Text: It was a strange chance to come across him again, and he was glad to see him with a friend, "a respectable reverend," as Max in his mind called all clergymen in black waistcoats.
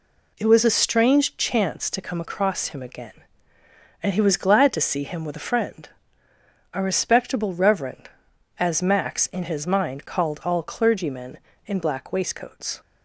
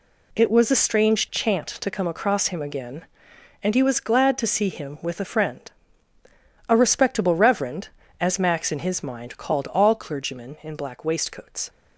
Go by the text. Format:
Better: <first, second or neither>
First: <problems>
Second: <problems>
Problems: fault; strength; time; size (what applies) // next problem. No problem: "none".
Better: first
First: none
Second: says "chant" for "chance"; at 1.3 s